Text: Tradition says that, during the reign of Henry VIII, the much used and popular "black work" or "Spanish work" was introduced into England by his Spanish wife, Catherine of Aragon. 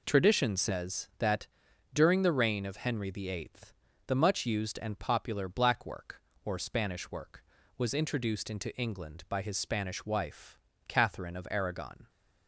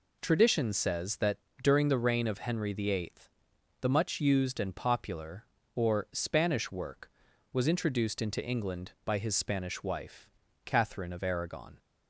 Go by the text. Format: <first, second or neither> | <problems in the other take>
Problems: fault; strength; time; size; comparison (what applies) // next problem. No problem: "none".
first | skips "black work"; at 5.6 s